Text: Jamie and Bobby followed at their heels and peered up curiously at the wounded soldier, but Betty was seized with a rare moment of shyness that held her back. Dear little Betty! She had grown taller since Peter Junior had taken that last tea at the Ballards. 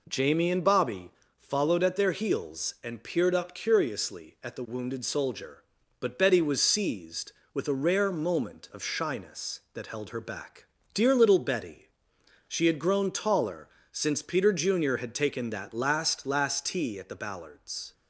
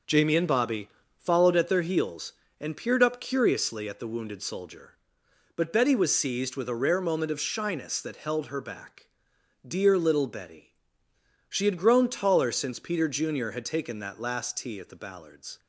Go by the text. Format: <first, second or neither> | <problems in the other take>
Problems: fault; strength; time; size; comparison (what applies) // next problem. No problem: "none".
second | pauses between "Bobby" and "followed"; slight; at 1.1 s; 0.28 s long; slight in the second // pauses between "taller" and "since"; slight; at 13.6 s; 0.26 s long // says "last" twice; at 16.2 s